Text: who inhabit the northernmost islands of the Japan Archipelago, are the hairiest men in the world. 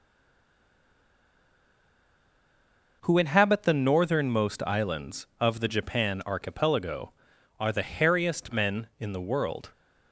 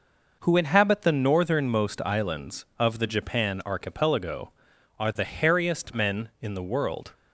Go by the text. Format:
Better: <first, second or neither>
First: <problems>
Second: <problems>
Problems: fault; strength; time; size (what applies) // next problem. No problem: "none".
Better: second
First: stays silent before the first word; strong; until 3.0 s; 3.0 s long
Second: none